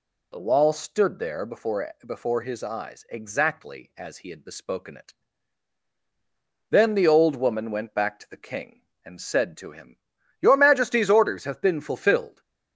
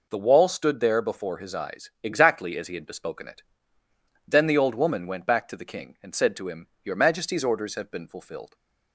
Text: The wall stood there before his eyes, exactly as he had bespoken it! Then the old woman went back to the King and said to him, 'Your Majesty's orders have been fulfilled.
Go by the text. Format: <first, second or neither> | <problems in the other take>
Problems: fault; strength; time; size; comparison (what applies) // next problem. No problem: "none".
second | says "before" twice; at 2.0 s